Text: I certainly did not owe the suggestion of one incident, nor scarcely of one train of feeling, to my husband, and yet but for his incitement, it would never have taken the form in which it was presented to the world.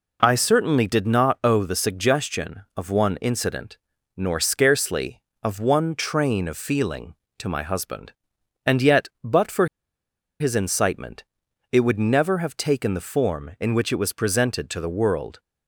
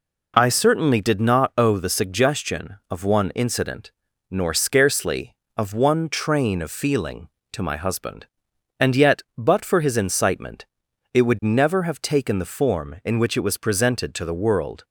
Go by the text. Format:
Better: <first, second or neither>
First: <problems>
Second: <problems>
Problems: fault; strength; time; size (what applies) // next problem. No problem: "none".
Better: second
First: pauses between "for" and "his"; noticeable; at 9.6 s; 0.75 s long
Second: none